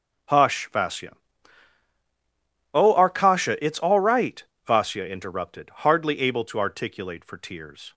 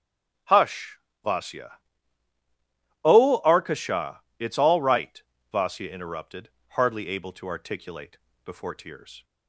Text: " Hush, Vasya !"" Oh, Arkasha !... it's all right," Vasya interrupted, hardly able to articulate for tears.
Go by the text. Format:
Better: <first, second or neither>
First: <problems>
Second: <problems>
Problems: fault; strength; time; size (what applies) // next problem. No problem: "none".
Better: first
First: none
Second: says "before" for "for"; at 8.4 s